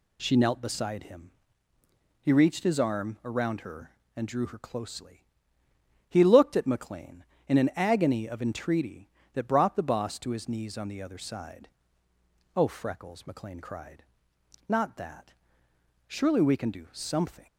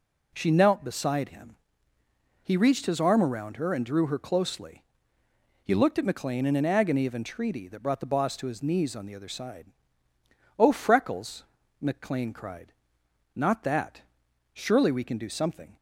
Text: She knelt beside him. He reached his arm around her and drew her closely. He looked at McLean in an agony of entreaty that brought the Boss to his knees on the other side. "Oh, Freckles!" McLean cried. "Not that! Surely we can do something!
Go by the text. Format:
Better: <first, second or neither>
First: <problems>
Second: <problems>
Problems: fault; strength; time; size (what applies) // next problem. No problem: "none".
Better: neither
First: none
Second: none